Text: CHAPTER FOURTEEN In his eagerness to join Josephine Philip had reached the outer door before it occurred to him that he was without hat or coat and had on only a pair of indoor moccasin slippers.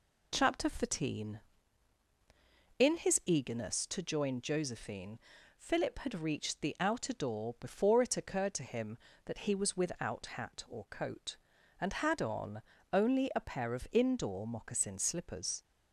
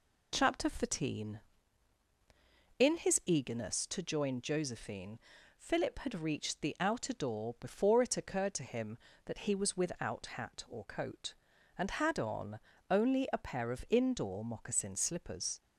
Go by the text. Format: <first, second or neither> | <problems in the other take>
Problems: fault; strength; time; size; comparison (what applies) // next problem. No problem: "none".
neither | pauses between "Josephine" and "Philip"; the same in both // pauses between "on" and "only"; slight; the same in both